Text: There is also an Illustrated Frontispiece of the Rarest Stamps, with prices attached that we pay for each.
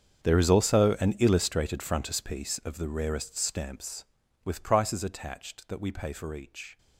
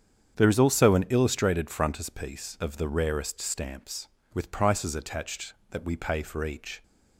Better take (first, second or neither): second